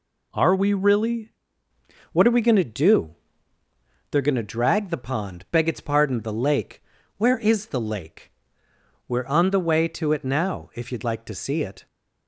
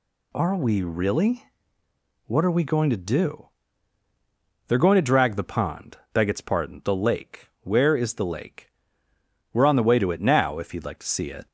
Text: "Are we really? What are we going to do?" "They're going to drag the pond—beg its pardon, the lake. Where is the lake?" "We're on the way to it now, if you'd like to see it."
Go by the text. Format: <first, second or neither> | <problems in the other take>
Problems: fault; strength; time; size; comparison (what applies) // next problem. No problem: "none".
second | changes voice at "What"; from 2.1 s on; 9.7 s long